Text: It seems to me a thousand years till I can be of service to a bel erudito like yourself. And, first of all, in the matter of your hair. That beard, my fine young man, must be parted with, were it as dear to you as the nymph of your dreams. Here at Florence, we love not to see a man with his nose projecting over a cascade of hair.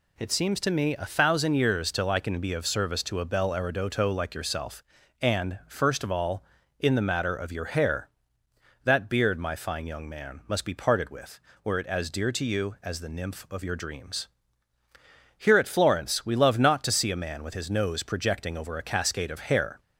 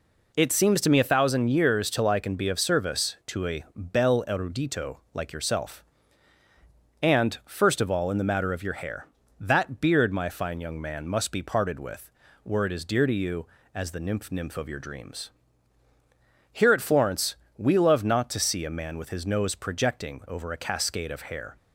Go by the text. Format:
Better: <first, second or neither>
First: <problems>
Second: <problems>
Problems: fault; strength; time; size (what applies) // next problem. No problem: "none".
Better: first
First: none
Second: pauses between "erudito" and "like"; slight; at 4.9 s; 0.16 s long // says "nymph" twice; at 14.3 s